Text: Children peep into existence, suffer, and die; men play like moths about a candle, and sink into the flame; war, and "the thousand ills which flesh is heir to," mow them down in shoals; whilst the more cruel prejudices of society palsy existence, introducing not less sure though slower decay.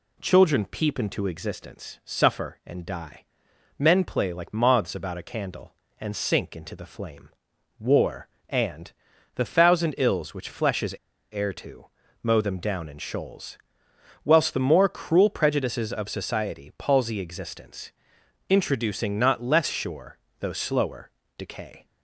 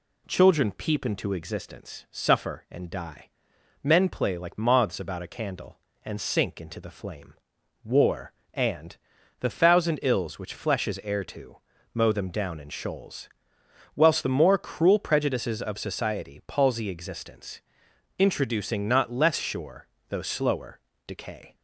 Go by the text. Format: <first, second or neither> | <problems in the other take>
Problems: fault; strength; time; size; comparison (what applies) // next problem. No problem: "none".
second | pauses between "and" and "the"; at 8.9 s; 0.44 s long; also in the second // pauses between "is" and "heir"; slight; at 10.9 s; 0.35 s long // pauses between "sure" and "though"; slight; at 20.1 s; 0.24 s long; slight in the second // pauses between "slower" and "decay"; slight; at 21.1 s; 0.26 s long; slight in the second